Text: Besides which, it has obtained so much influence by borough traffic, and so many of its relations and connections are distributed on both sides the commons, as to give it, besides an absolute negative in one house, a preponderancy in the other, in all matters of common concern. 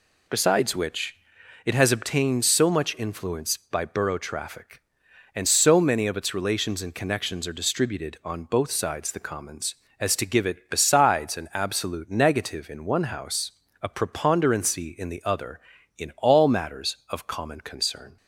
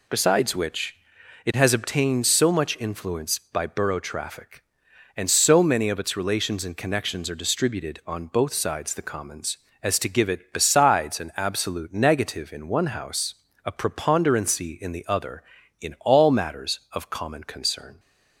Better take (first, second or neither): neither